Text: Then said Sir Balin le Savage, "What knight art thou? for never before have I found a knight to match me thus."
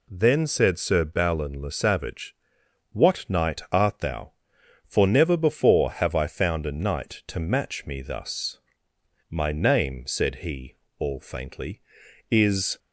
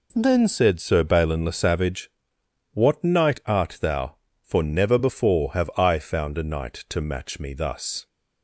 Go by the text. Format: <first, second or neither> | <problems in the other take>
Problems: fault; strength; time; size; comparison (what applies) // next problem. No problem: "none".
second | goes on to say "My name said he all faintly is"; strong; from 9.3 s on; 3.4 s long